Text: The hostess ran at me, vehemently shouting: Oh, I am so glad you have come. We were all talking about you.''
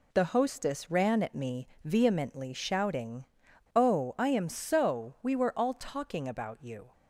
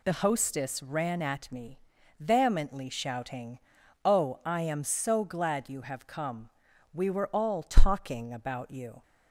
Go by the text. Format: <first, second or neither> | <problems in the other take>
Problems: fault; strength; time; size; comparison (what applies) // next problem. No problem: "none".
second | skips "glad you have come"; at 5.1 s